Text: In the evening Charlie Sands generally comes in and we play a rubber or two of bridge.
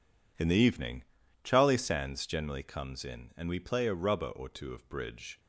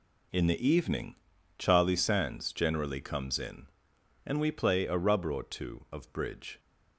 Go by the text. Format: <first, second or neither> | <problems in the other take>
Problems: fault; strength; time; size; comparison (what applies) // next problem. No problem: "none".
neither | pauses between "evening" and "Charlie"; the same in both